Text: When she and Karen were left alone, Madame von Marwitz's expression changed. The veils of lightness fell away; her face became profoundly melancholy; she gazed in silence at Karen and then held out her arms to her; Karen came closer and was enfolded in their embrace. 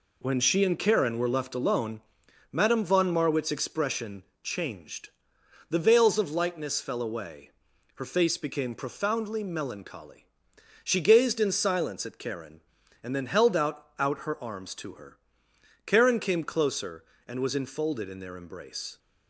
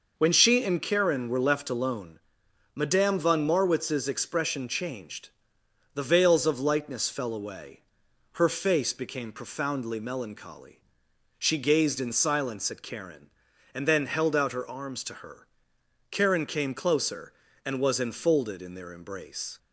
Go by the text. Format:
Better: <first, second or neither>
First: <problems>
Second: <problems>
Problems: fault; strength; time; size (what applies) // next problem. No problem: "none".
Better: second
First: pauses between "expression" and "changed"; slight; at 4.2 s; 0.22 s long // says "out" twice; at 13.9 s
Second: none